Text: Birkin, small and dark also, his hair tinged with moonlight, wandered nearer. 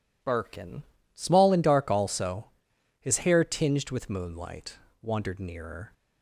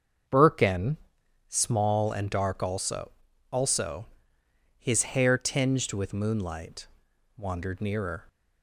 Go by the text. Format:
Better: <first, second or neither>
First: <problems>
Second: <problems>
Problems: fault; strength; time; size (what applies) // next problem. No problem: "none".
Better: first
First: none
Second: starts louder than the rest; until 1.8 s; 6.5 dB // says "also" twice; at 3.5 s